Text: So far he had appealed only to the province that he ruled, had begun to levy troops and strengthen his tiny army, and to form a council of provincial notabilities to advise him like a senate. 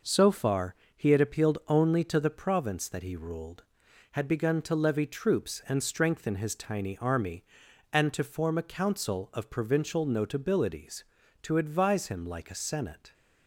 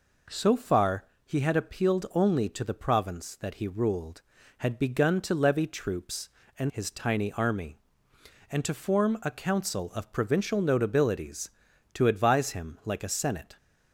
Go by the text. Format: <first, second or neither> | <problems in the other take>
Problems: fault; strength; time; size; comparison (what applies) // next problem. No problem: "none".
first | pauses between "far" and "he"; slight; at 1.0 s; 0.20 s long; slight in the first // skips "strengthen"; at 6.6 s